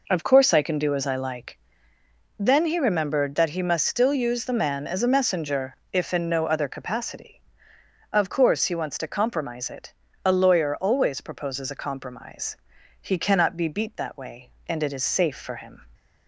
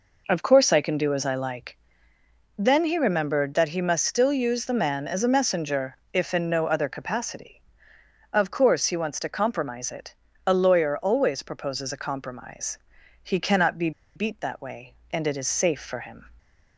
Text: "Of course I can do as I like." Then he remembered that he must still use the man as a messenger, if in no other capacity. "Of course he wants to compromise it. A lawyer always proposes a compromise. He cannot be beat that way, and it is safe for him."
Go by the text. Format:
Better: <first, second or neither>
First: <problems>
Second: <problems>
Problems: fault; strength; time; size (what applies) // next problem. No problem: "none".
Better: first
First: none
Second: pauses between "be" and "beat"; slight; at 13.9 s; 0.25 s long